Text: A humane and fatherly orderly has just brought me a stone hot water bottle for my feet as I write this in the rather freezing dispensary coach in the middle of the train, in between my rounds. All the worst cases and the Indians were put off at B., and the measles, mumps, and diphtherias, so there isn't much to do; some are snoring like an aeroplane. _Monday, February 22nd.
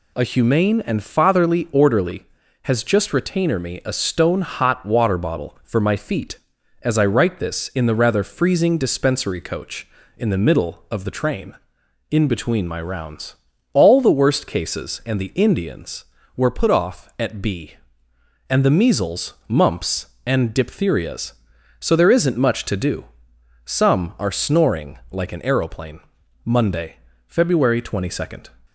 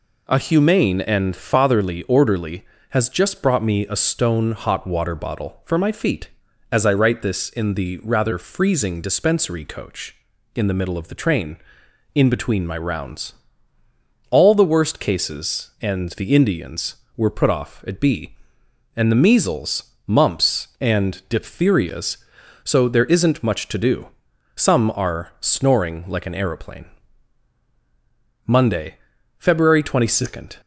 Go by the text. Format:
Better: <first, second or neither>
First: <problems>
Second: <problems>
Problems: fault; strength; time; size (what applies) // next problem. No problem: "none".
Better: second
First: says "retainer" for "brought"; at 3.1 s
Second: none